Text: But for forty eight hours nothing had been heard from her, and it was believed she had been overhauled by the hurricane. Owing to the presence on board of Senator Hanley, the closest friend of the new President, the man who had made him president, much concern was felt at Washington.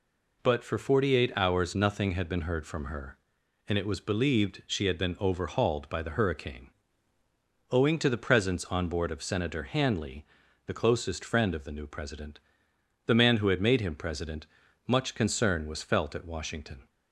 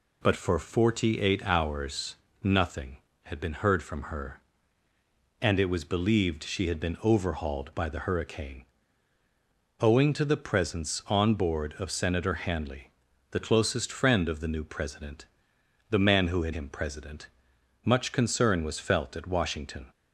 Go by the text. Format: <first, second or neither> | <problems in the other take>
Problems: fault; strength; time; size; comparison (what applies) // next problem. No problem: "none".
first | pauses between "hours" and "nothing"; slight; at 2.1 s; 0.30 s long // skips "made"; at 16.5 s